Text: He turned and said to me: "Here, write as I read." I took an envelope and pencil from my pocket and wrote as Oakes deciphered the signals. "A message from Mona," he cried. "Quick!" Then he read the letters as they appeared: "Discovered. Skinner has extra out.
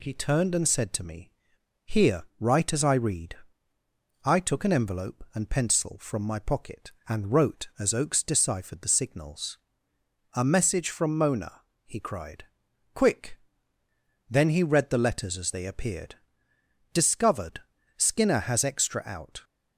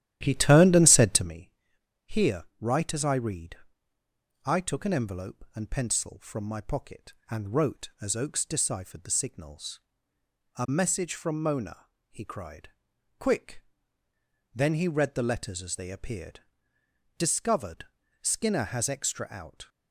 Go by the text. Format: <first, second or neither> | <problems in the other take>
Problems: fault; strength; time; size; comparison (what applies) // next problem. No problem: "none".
first | starts louder than the rest; strong; until 1.4 s; 12.5 dB